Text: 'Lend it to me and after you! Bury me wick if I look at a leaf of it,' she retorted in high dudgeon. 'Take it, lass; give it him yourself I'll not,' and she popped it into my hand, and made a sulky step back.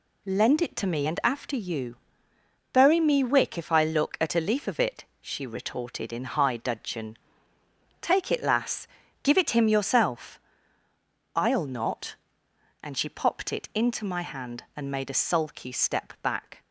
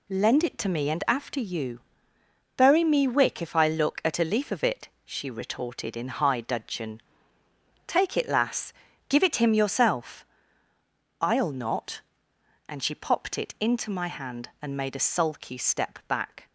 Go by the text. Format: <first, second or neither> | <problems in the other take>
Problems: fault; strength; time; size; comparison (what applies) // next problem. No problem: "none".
neither | pauses between "yourself" and "I'll"; noticeable; the same in both